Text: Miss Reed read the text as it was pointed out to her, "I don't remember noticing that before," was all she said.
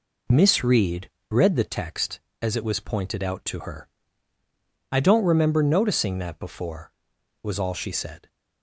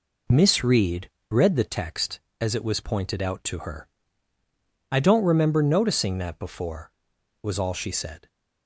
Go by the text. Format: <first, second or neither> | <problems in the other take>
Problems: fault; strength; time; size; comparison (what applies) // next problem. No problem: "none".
neither | pauses between "Reed" and "read"; slight; the same in both